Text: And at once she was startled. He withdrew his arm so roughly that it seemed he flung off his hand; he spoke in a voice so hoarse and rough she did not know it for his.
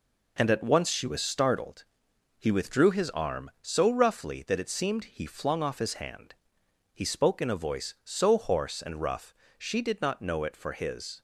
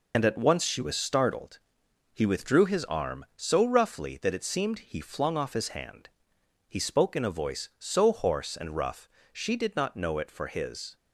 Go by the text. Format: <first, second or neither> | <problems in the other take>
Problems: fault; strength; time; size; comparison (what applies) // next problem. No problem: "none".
first | loses the start of "And"; at 0.1 s; 40 ms // pauses between "rough" and "she"; slight; at 9.0 s; 0.24 s long; slight in the first